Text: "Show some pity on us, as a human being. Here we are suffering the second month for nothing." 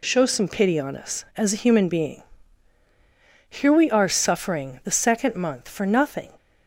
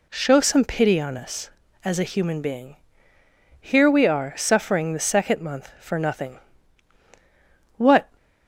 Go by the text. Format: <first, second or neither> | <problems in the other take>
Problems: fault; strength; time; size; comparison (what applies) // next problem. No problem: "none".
first | goes on to say "What"; slight; from 7.7 s on; 0.32 s long